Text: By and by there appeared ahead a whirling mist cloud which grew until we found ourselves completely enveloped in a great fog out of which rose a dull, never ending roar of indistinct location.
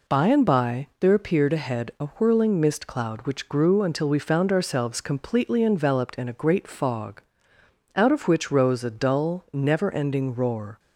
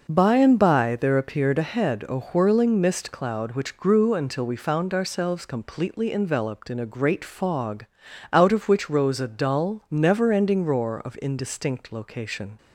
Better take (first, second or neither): second